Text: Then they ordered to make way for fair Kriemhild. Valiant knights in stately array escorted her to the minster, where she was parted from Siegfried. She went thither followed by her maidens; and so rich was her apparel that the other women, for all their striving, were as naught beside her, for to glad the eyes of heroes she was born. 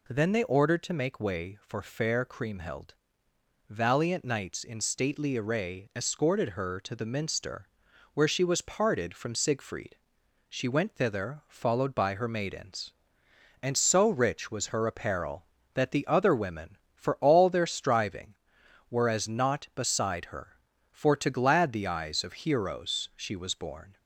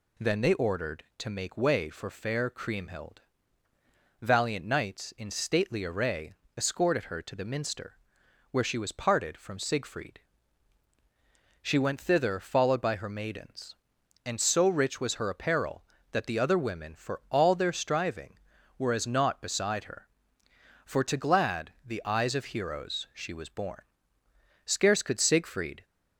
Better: first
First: none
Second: pauses between "array" and "escorted"; slight; at 6.3 s; 0.24 s long // goes on to say "Scarce could Siegfried"; noticeable; from 24.6 s on; 1.2 s long

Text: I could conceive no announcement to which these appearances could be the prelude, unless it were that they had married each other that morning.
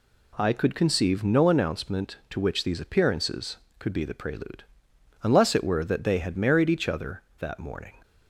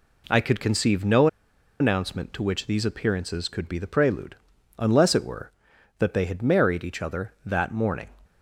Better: first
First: none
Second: pauses between "no" and "announcement"; noticeable; at 1.2 s; 0.53 s long

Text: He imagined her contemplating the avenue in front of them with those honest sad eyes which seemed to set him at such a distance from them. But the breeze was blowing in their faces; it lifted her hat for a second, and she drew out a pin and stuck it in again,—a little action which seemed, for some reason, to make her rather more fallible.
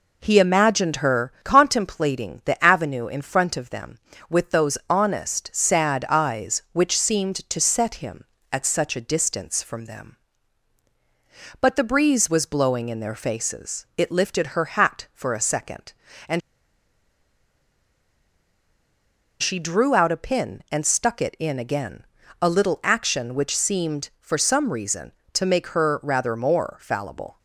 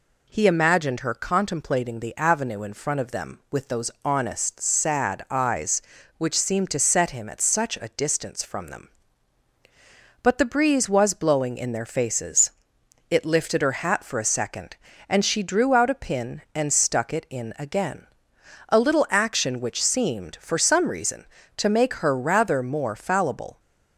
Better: second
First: pauses between "and" and "she"; strong; at 16.4 s; 3.0 s long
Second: none

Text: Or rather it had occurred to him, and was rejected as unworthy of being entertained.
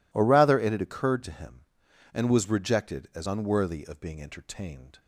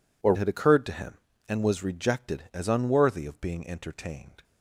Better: first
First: none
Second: skips "rather it"; at 0.3 s

